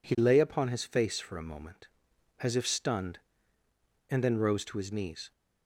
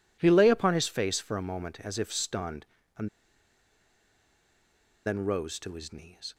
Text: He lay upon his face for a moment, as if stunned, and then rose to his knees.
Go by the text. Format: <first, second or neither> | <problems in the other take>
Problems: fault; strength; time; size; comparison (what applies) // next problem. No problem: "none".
first | pauses between "and" and "then"; strong; at 3.0 s; 1.9 s long